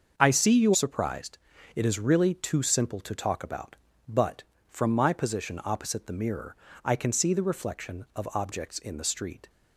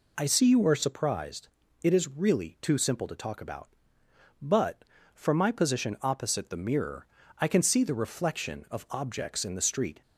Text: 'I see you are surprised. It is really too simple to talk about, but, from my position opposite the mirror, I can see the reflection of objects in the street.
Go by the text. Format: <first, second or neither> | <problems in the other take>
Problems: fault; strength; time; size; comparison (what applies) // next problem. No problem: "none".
second | starts louder than the rest; until 1.1 s; 6.5 dB // skips "are"; at 0.7 s